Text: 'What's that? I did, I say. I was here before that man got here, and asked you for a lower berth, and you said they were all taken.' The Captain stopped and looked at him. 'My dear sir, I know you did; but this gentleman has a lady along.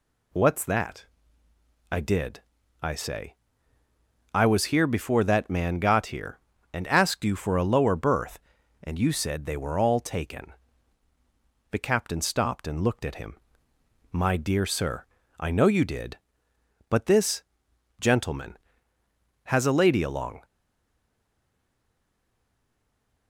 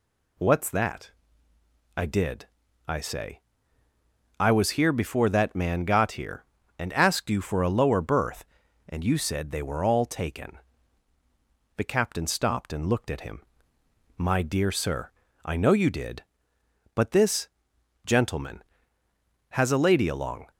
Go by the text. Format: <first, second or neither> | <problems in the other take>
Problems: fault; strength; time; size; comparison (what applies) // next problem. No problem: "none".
second | pauses between "this" and "gentleman"; noticeable; at 17.4 s; 0.58 s long; noticeable in the second // stays silent after the last word; strong; from 20.4 s on; 2.8 s long